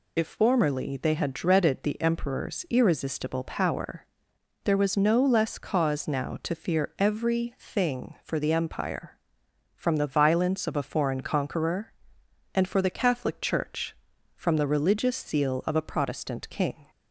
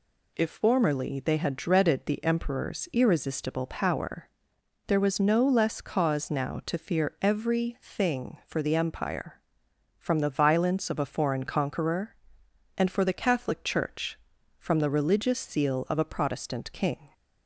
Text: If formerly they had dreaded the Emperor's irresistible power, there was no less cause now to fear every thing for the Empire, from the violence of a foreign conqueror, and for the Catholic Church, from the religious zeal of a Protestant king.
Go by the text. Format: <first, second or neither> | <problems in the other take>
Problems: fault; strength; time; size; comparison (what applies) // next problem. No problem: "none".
second | loses the start of "If"; at 0.1 s; 40 ms